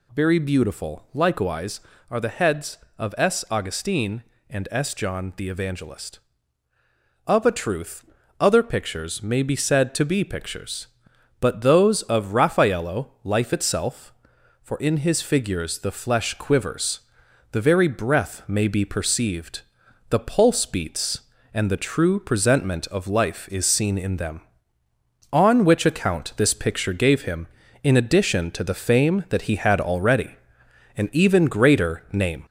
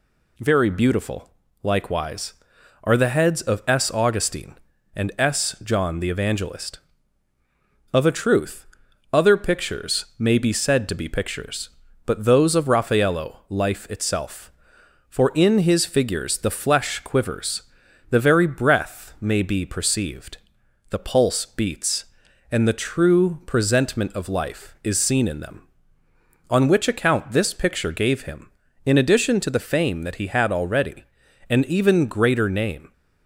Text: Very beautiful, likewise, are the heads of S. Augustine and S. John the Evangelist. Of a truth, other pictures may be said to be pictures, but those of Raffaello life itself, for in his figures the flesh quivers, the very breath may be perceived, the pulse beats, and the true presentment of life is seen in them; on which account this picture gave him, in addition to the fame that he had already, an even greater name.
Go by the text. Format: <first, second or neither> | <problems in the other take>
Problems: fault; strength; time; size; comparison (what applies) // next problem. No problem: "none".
second | gets louder; noticeable; throughout; 4 dB